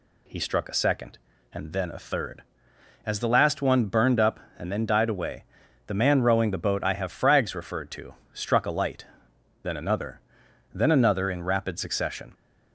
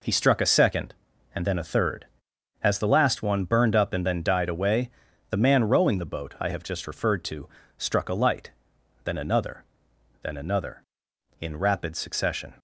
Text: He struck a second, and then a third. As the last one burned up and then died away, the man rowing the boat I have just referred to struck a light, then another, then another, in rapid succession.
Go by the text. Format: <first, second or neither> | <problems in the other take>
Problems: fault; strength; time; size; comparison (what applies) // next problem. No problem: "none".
second | says "frags" for "just"; at 7.1 s // pauses between "to" and "struck"; slight; at 8.1 s; 0.20 s long; slight in the second